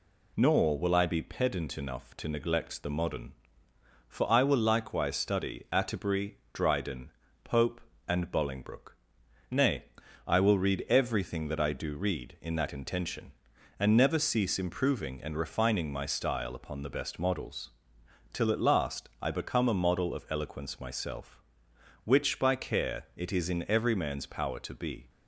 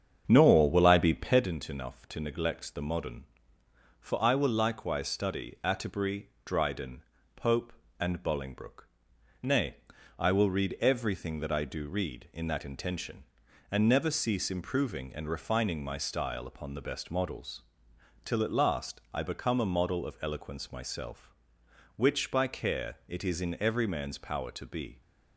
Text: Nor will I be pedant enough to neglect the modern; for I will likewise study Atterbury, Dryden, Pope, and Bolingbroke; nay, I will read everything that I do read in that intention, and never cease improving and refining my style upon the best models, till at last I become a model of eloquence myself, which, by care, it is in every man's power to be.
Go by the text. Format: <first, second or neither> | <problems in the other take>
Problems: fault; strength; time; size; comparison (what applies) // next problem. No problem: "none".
first | starts louder than the rest; strong; until 1.5 s; 8 dB